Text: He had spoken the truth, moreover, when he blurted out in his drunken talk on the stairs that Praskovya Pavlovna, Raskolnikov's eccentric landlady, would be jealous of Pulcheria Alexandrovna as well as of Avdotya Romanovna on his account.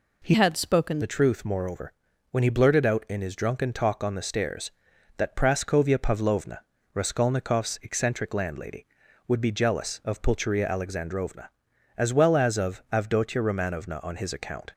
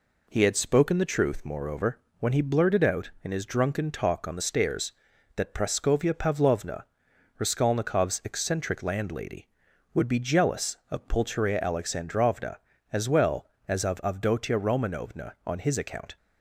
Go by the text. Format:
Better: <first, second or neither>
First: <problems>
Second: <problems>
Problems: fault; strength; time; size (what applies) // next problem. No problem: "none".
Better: second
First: changes voice from "had" to "spoken"; from 0.3 to 1.0 s; 0.7 s long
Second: none